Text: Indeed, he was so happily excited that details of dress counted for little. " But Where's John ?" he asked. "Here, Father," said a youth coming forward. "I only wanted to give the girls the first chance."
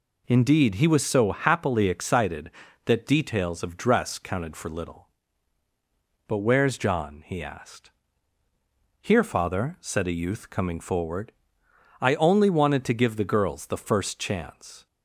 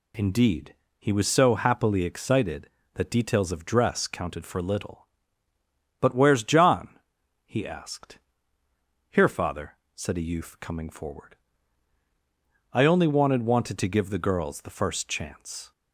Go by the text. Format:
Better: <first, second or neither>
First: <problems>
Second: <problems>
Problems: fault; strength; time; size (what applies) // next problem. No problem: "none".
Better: first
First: none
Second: says "wanted" twice; at 13.4 s